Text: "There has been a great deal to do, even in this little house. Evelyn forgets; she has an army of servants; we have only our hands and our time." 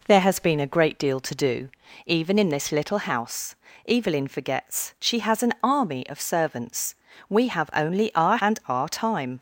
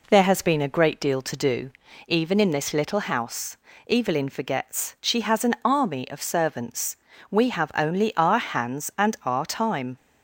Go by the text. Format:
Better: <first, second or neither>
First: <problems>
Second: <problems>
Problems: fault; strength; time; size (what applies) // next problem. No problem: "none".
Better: second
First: skips "hands"; at 8.3 s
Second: none